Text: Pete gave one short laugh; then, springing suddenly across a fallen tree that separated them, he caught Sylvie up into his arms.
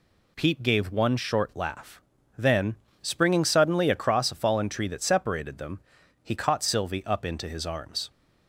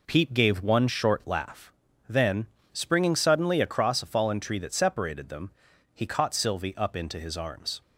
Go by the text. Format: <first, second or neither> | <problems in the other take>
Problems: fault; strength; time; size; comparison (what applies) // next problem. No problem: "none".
first | starts louder than the rest; noticeable; until 1.6 s; 4 dB